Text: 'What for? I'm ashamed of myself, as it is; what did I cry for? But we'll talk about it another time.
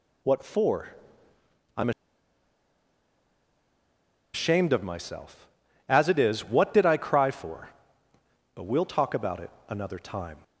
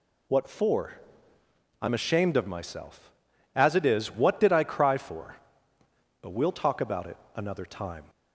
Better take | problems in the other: second | pauses between "I'm" and "ashamed"; strong; at 1.8 s; 2.4 s long // pauses between "it" and "another"; slight; at 9.5 s; 0.18 s long; slight in the second

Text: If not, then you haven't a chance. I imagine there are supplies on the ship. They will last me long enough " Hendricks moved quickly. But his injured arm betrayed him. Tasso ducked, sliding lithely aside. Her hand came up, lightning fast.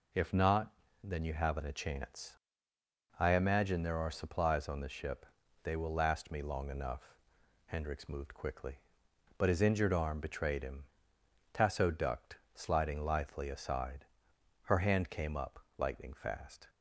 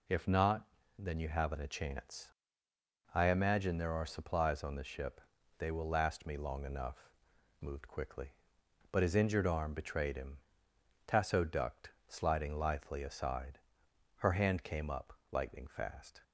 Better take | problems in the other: first | skips "Hendricks"; at 7.6 s

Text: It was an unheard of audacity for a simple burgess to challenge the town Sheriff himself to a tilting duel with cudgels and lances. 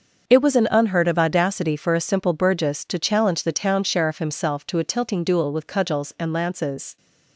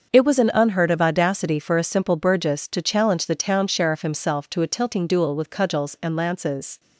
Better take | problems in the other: neither | starts louder than the rest; the same in both

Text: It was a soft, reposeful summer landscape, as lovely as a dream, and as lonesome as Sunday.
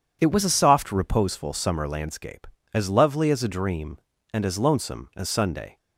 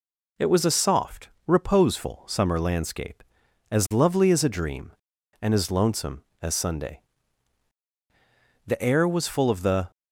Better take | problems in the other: first | goes on to say "The air was full of the"; noticeable; from 8.6 s on; 1.2 s long

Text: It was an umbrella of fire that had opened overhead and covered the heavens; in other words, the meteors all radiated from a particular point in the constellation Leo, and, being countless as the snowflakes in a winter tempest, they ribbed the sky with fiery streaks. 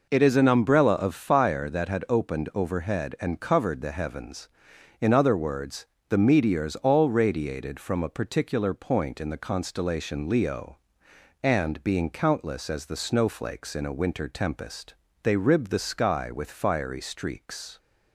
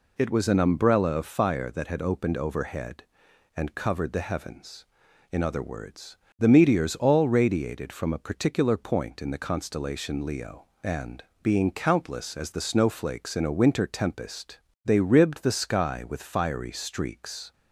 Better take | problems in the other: second | says "is" for "was"; at 0.2 s

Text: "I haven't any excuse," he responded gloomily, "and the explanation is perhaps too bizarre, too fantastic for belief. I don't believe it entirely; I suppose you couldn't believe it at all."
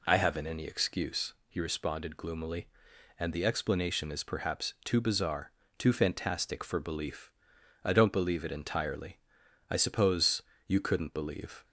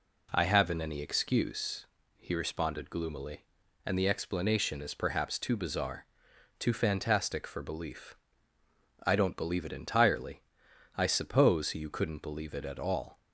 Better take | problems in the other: second | pauses between "suppose" and "you"; slight; at 10.4 s; 0.24 s long // stops before "it at all"; at 11.6 s

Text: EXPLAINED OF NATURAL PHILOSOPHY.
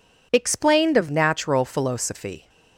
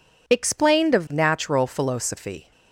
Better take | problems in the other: neither | none

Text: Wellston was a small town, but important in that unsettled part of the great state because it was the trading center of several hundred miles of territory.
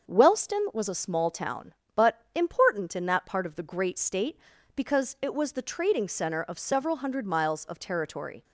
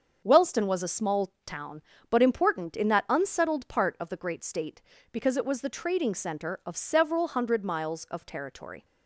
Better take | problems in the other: second | starts louder than the rest; until 1.1 s; 6.5 dB; also in the second // skips "unsettled"; at 3.2 s

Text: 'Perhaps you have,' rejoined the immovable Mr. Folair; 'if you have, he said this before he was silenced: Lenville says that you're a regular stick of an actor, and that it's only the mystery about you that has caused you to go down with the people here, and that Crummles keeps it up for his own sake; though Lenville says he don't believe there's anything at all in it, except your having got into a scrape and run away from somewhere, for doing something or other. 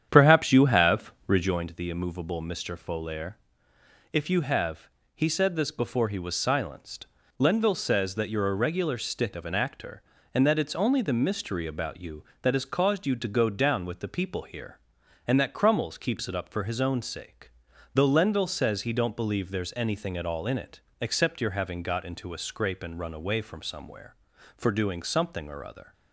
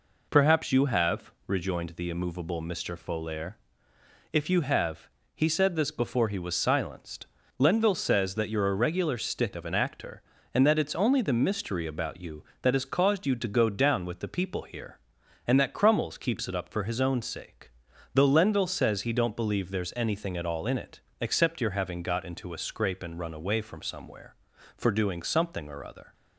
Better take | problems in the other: second | starts louder than the rest; strong; until 1.6 s; 9 dB

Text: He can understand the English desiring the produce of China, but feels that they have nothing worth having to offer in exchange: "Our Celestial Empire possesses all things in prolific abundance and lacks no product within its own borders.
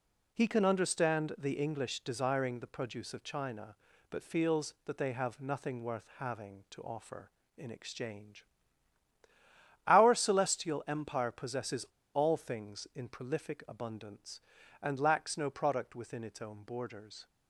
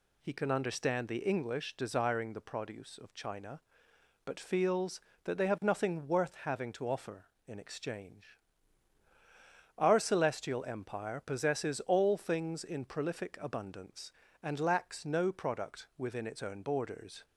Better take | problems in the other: second | pauses between "possesses" and "all"; slight; at 11.8 s; 0.30 s long

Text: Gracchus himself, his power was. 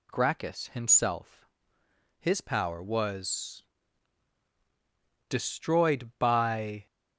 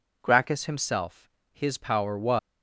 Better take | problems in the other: second | goes on to say "destroyed by"; from 5.2 s on; 1.5 s long

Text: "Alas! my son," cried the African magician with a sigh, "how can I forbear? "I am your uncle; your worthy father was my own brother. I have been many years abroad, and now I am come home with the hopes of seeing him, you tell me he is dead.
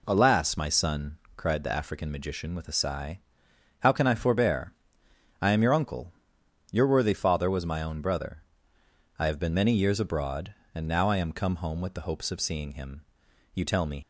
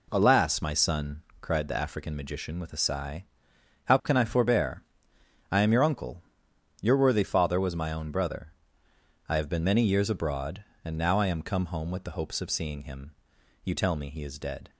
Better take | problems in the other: second | stops before "he is dead"; at 14.0 s

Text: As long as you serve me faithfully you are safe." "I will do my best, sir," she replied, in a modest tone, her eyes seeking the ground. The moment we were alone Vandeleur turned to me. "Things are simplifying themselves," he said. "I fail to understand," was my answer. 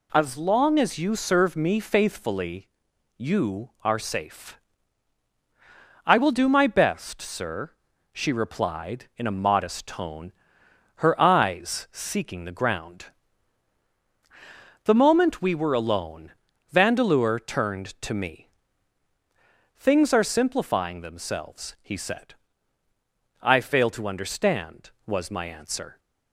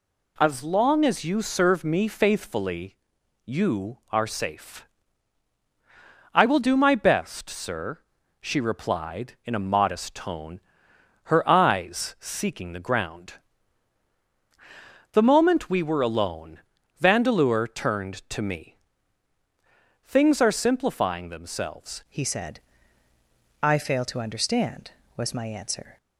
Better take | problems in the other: first | pauses between "faithfully" and "you"; noticeable; at 2.9 s; 0.52 s long; noticeable in the first // pauses between "alone" and "Vandeleur"; at 16.5 s; 0.40 s long; also in the first // changes voice at "he"; from 22.0 s on; 3.9 s long

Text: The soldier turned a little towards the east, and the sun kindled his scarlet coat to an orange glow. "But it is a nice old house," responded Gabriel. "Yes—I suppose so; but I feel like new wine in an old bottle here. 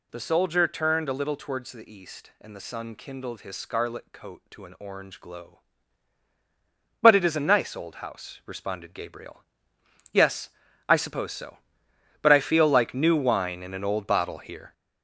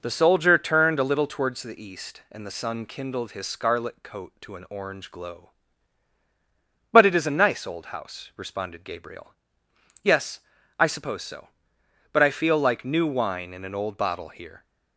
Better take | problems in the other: second | gets louder; noticeable; throughout; 6 dB

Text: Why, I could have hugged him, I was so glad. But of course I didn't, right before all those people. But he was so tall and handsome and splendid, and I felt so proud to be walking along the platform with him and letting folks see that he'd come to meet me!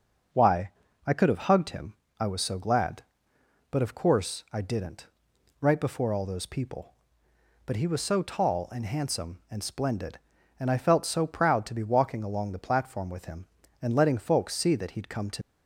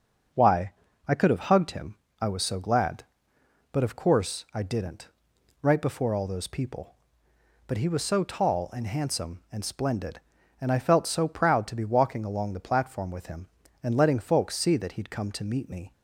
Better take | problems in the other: second | starts louder than the rest; until 1.6 s; 6 dB; also in the second // stops before "meet me"; at 15.4 s

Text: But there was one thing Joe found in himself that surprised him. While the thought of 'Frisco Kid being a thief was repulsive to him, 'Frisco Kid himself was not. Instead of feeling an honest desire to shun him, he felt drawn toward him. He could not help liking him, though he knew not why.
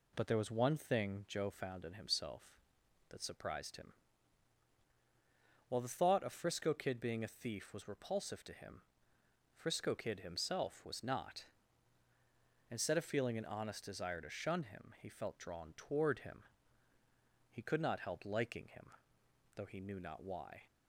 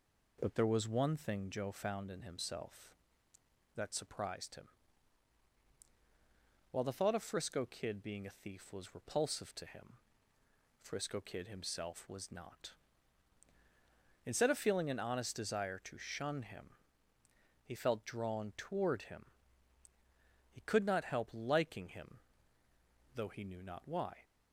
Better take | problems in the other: neither | none

